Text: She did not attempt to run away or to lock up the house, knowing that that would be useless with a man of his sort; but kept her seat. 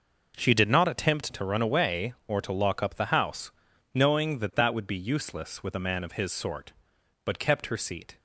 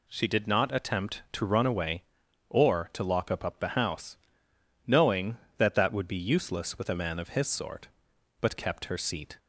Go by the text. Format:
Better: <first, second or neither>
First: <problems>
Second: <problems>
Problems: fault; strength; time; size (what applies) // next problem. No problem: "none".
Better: first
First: none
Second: says "up" twice; at 3.4 s